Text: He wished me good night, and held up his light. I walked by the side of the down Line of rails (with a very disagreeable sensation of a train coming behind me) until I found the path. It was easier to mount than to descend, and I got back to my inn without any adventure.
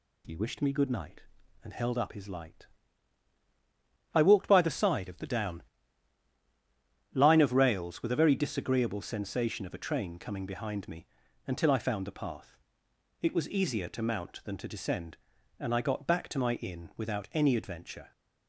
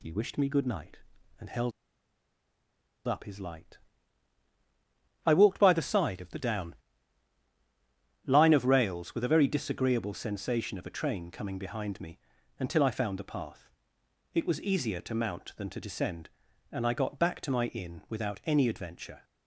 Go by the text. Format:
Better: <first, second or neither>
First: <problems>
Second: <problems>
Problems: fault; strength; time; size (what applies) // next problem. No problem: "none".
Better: first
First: pauses between "down" and "Line"; strong; at 5.6 s; 1.5 s long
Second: pauses between "held" and "up"; strong; at 1.7 s; 1.3 s long // pauses between "down" and "Line"; strong; at 6.7 s; 1.5 s long